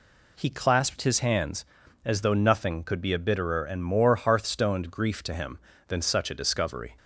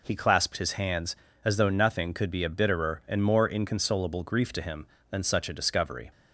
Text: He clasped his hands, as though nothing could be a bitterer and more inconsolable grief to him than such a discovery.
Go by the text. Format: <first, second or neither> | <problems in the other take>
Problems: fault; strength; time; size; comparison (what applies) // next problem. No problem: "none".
second | says "hearthstoned" for "inconsolable"; at 4.1 s